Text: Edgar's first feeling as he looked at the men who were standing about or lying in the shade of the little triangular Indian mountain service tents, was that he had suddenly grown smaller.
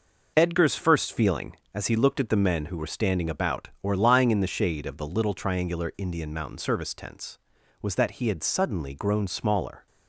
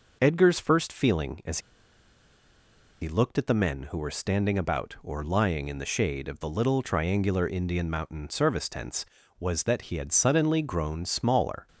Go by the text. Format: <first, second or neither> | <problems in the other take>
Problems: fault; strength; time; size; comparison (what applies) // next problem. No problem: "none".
first | pauses between "as" and "he"; strong; at 1.5 s; 1.4 s long